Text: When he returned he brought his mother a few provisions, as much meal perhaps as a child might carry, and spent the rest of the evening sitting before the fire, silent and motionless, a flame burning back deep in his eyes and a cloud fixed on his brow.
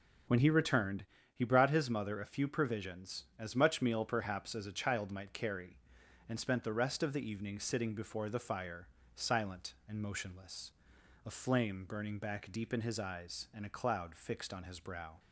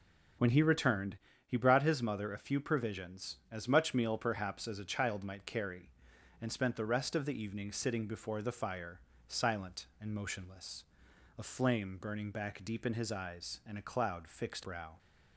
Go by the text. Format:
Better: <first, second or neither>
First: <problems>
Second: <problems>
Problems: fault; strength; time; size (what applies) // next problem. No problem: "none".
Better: first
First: pauses between "returned" and "he"; slight; at 1.0 s; 0.28 s long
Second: pauses between "returned" and "he"; slight; at 1.1 s; 0.28 s long // skips "on his"; at 14.6 s